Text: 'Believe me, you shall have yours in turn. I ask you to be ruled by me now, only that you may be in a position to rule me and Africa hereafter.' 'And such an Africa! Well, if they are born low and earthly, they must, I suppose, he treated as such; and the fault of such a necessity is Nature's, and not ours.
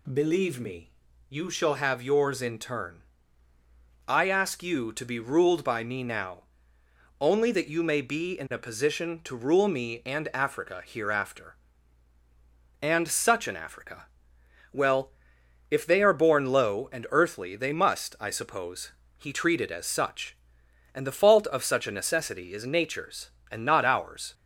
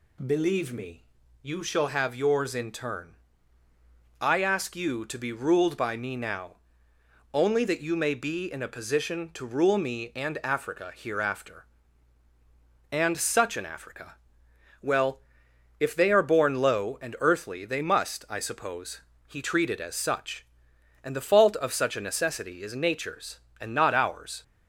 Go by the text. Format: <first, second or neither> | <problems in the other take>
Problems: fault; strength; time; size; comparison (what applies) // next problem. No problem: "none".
neither | none